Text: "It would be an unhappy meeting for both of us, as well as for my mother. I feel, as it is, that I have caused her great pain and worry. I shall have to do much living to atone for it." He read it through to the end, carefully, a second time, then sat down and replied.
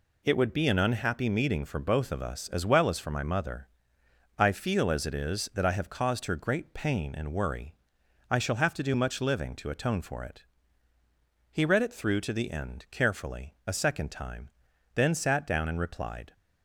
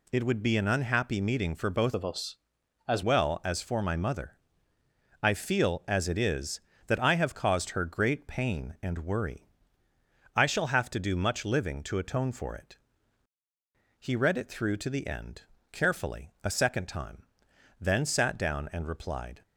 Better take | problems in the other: first | changes voice from "of" to "as"; from 1.9 to 3.0 s; 1.1 s long

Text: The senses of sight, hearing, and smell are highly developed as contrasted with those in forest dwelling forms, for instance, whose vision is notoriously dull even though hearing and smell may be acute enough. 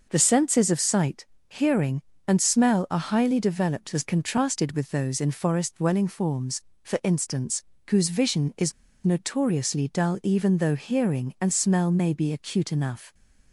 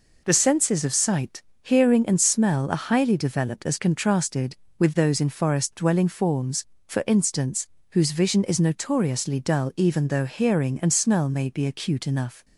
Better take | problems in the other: second | pauses between "is" and "notoriously"; slight; at 8.7 s; 0.33 s long

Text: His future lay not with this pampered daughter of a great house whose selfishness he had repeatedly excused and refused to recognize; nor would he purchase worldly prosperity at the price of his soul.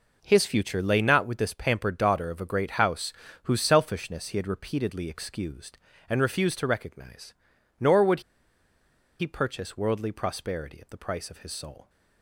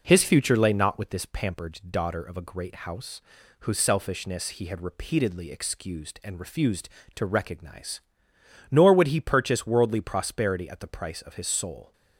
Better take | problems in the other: second | pauses between "house" and "whose"; slight; at 3.1 s; 0.32 s long; also in the second // pauses between "would" and "he"; at 8.2 s; 0.99 s long

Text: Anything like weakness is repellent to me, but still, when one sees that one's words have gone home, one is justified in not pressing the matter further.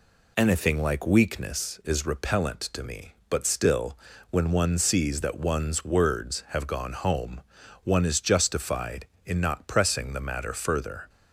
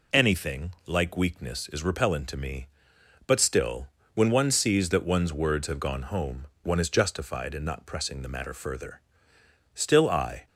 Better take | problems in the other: first | pauses between "Anything" and "like"; slight; at 0.7 s; 0.16 s long // goes on to say "Still I"; noticeable; from 9.7 s on; 0.72 s long

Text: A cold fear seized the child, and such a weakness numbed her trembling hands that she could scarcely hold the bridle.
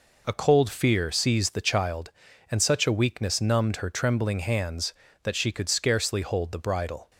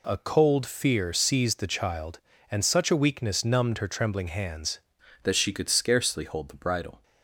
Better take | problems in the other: first | changes voice at "that"; from 5.2 s on; 1.8 s long

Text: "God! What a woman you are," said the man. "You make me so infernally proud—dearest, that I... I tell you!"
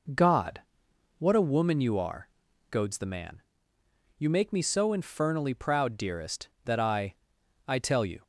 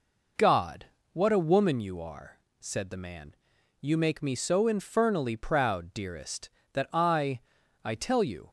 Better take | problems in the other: second | says "goads" for "said"; at 2.7 s

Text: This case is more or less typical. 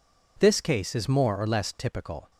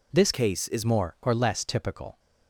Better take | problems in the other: first | changes voice from "case" to "is"; from 0.3 to 0.8 s; 0.5 s long

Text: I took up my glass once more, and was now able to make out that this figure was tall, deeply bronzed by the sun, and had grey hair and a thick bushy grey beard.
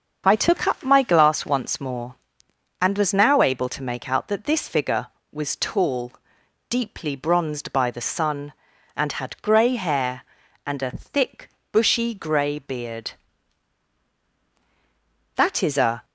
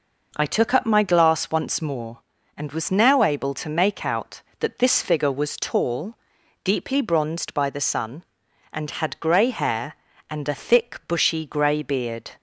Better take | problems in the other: second | starts louder than the rest; until 1.2 s; 6.5 dB // pauses between "thick" and "bushy"; slight; at 11.5 s; 0.22 s long // goes on to say "That is a"; noticeable; from 15.3 s on; 0.68 s long

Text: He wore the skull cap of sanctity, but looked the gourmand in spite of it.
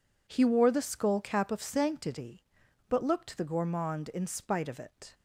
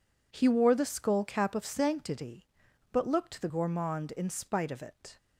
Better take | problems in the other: neither | none

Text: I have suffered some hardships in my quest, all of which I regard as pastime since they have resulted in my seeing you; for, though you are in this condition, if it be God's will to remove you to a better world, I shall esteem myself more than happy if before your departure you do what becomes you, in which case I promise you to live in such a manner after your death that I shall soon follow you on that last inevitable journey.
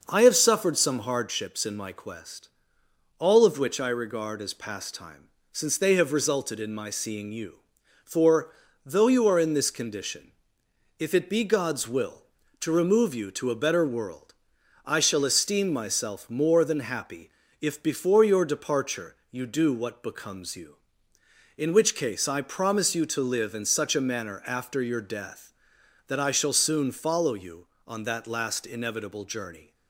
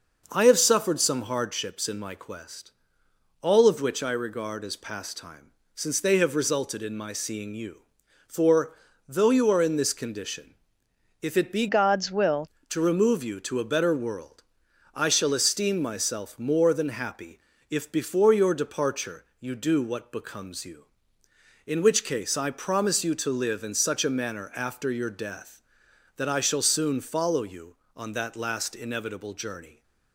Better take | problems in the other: first | pauses between "pastime" and "since"; slight; at 5.5 s; 0.26 s long; slight in the first // changes voice from "God's" to "will"; from 11.6 to 12.4 s; 0.8 s long // pauses between "happy" and "if"; slight; at 17.3 s; 0.32 s long; slight in the first

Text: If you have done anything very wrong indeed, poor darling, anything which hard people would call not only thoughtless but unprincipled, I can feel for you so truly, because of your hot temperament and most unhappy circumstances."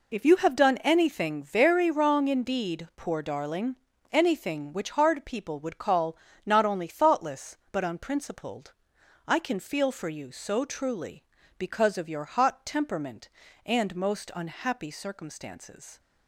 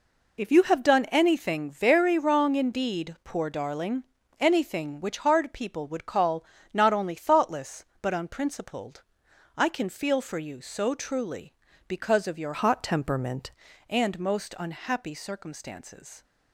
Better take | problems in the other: first | pauses between "call" and "not"; slight; at 6.4 s; 0.28 s long; slight in the first // changes voice from "hot" to "temperament"; from 12.5 to 13.5 s; 1.0 s long

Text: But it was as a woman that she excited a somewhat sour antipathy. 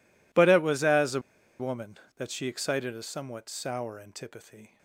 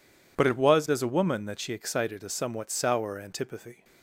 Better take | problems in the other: second | pauses between "a" and "woman"; at 1.1 s; 0.39 s long

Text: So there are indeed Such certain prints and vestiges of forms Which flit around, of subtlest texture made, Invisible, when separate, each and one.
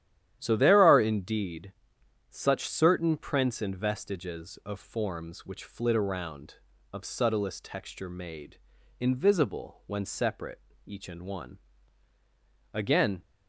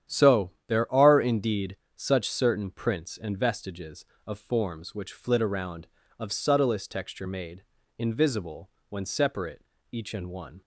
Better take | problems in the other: second | starts louder than the rest; strong; until 1.4 s; 11.5 dB; strong in the second // pauses between "indeed" and "Such"; noticeable; at 1.7 s; 0.58 s long; slight in the second // goes on to say "Again"; slight; from 12.7 s on; 0.48 s long

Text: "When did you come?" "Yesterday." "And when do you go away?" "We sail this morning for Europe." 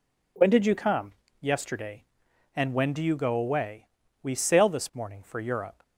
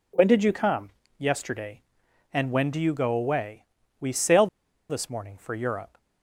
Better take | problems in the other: first | pauses between "sail" and "this"; at 4.4 s; 0.43 s long

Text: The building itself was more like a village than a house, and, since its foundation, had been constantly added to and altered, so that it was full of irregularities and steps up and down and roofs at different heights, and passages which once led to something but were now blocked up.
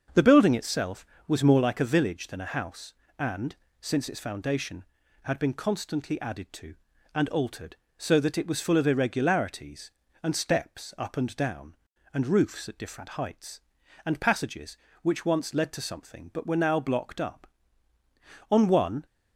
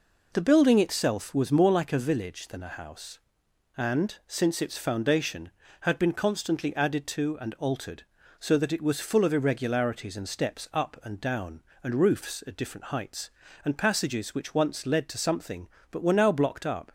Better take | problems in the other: second | starts louder than the rest; until 1.3 s; 6.5 dB // goes on to say "On one"; from 18.5 s on; 0.54 s long

